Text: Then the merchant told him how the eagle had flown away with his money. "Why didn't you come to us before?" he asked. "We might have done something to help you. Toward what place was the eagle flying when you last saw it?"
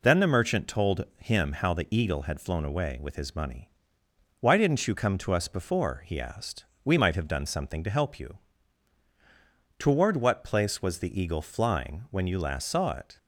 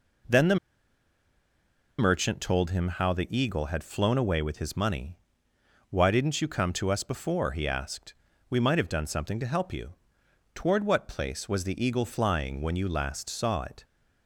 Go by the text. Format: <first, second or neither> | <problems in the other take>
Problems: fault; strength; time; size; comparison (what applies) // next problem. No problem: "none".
first | pauses between "the" and "merchant"; strong; at 0.5 s; 1.4 s long